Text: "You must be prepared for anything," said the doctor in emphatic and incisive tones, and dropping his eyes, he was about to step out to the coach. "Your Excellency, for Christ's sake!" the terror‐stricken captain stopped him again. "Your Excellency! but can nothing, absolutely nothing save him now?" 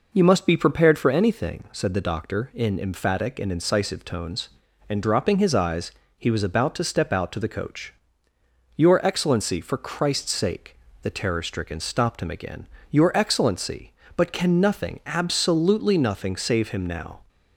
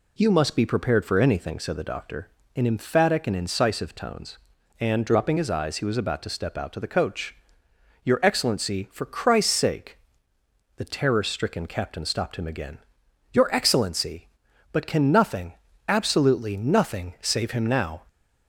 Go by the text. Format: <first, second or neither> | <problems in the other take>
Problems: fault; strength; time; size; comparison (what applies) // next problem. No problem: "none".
second | skips "captain"; at 11.7 s